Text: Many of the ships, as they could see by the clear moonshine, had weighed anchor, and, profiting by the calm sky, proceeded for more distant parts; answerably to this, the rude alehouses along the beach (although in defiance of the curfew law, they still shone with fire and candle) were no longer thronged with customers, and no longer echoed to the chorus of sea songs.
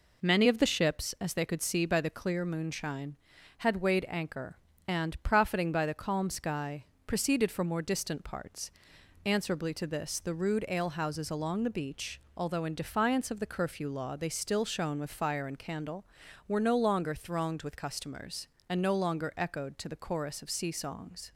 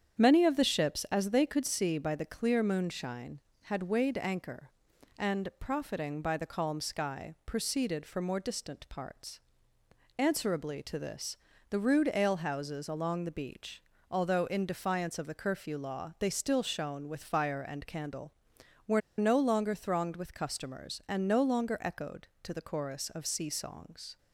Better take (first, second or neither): first